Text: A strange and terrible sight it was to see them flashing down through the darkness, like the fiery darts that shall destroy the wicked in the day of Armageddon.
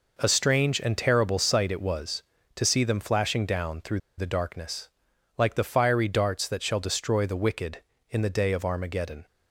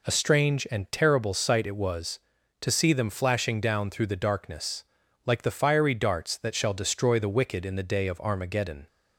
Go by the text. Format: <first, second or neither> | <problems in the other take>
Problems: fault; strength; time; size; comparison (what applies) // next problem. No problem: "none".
second | pauses between "through" and "the"; slight; at 3.9 s; 0.18 s long